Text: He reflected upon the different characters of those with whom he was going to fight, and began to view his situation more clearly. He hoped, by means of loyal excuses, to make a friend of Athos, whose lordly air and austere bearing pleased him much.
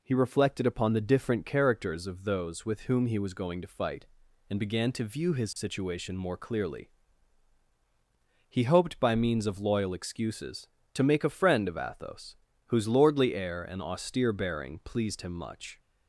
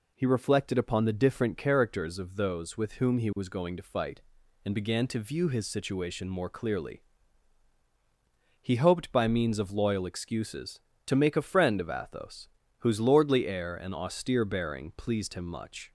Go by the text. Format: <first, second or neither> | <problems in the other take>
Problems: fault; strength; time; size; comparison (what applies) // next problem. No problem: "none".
neither | none